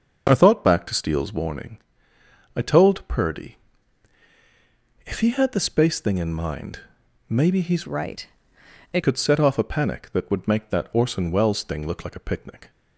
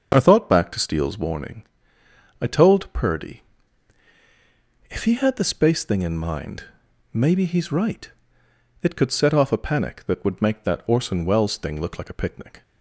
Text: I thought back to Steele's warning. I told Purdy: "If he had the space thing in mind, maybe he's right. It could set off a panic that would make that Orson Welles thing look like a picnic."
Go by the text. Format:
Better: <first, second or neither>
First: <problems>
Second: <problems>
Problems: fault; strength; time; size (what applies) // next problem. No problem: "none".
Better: second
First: starts louder than the rest; until 1.3 s; 6 dB // changes voice from "right" to "It"; from 7.8 to 9.0 s; 1.2 s long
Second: starts louder than the rest; until 1.1 s; 6.5 dB